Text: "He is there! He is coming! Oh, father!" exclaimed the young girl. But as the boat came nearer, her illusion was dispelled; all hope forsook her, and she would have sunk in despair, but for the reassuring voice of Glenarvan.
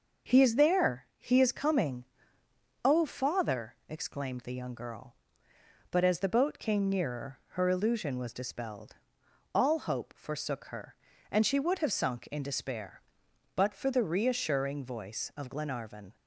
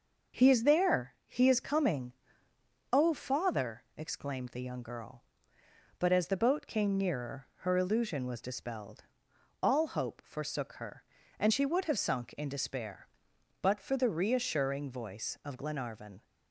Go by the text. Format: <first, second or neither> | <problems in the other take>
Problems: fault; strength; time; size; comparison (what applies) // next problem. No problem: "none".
neither | none